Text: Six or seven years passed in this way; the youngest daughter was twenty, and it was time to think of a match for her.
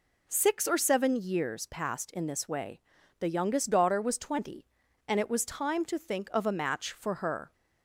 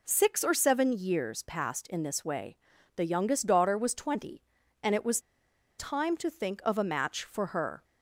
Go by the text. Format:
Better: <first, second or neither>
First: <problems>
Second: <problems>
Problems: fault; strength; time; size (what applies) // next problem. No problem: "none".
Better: first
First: none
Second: pauses between "was" and "time"; noticeable; at 5.1 s; 0.59 s long